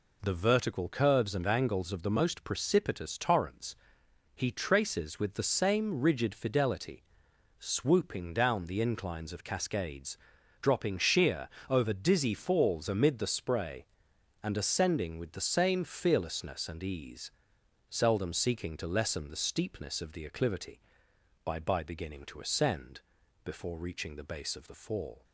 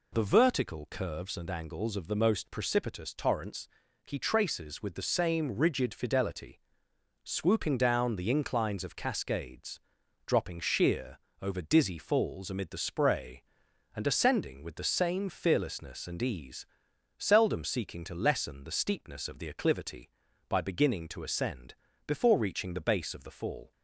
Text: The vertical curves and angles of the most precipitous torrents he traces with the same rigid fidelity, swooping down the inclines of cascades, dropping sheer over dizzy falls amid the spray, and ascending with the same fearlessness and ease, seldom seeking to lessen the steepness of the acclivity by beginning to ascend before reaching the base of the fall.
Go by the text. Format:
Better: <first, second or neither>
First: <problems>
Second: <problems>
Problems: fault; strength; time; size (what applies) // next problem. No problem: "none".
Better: second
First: pauses between "torrents" and "he"; noticeable; at 3.7 s; 0.60 s long // pauses between "sheer" and "over"; slight; at 11.4 s; 0.22 s long // says "by" twice; at 21.5 s // pauses between "ascend" and "before"; noticeable; at 22.9 s; 0.46 s long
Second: pauses between "torrents" and "he"; at 3.6 s; 0.38 s long // pauses between "sheer" and "over"; slight; at 11.1 s; 0.24 s long // pauses between "ascend" and "before"; slight; at 21.7 s; 0.32 s long